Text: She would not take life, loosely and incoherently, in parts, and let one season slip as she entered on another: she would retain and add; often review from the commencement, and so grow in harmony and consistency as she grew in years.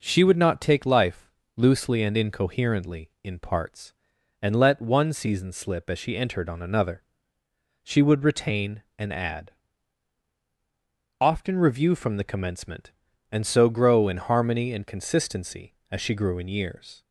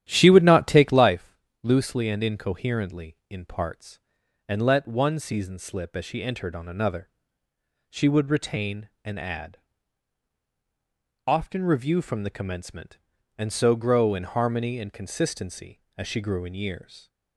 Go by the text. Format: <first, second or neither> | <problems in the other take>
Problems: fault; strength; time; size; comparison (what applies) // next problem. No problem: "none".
first | starts louder than the rest; strong; until 1.1 s; 11.5 dB